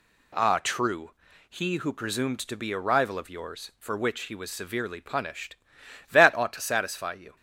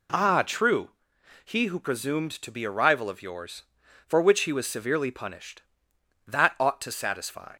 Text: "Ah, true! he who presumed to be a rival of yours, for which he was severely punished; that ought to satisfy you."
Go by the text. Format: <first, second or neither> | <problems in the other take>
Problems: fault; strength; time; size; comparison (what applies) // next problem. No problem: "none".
first | stops before "you"; at 7.5 s